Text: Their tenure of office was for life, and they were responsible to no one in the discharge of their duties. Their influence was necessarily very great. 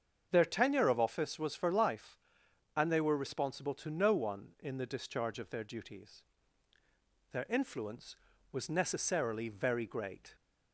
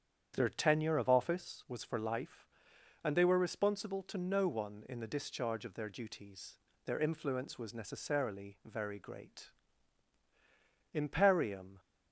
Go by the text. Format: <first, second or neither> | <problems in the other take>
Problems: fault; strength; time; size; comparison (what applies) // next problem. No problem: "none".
first | starts louder than the rest; strong; until 1.3 s; 8.5 dB; strong in the first // goes on to say "IMPERIUM"; noticeable; from 10.9 s on; 0.86 s long